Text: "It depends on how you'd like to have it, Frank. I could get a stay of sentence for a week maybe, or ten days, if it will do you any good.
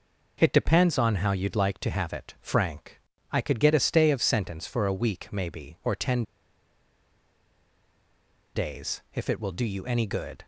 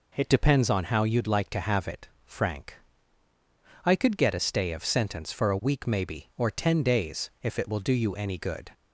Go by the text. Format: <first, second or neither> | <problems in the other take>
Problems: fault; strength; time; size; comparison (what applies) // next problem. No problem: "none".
second | pauses between "ten" and "days"; strong; at 6.2 s; 2.3 s long